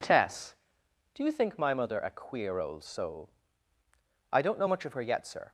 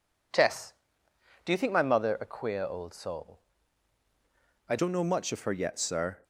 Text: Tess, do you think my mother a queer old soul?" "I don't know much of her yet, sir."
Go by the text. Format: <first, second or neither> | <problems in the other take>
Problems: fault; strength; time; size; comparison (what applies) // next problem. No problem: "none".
first | changes voice at "don't"; from 4.7 s on; 1.5 s long